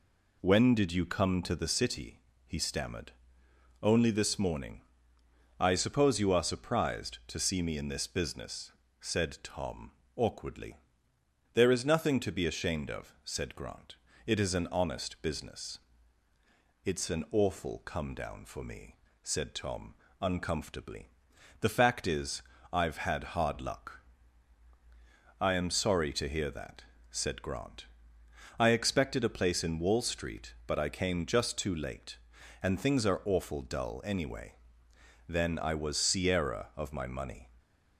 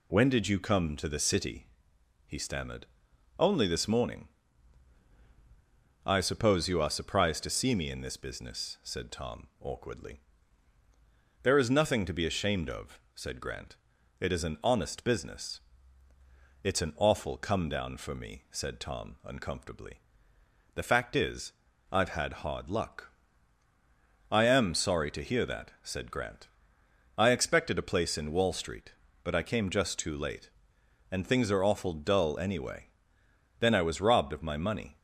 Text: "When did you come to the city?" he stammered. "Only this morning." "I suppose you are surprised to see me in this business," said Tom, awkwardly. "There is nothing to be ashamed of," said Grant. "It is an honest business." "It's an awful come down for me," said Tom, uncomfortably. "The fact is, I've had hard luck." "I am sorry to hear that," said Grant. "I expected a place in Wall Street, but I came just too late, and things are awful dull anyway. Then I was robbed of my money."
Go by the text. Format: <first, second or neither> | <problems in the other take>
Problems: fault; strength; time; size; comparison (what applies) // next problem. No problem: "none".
second | says "sierra" for "robbed"; at 35.9 s